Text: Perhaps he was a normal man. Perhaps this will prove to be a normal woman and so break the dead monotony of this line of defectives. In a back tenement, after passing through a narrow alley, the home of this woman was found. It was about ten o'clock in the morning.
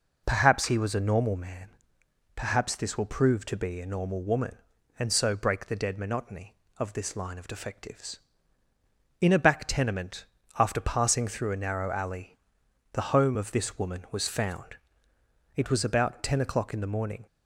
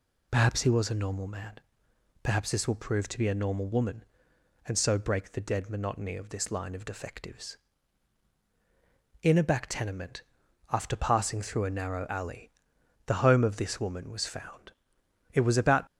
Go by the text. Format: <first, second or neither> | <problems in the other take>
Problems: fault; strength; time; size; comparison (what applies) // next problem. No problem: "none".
first | stops before "ten o'clock in the morning"; at 15.8 s